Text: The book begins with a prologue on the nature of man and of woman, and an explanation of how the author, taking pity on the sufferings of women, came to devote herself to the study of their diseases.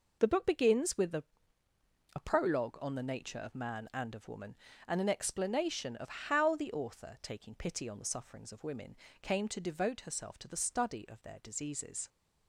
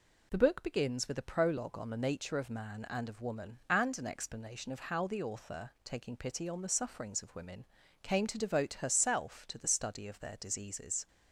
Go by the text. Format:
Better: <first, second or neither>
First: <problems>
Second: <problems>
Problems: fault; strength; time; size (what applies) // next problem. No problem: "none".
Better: second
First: says "a" twice; at 2.1 s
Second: none